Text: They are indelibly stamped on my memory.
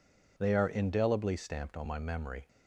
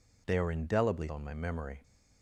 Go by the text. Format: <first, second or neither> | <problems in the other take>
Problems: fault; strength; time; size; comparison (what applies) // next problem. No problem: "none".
first | skips "stamped"; at 1.0 s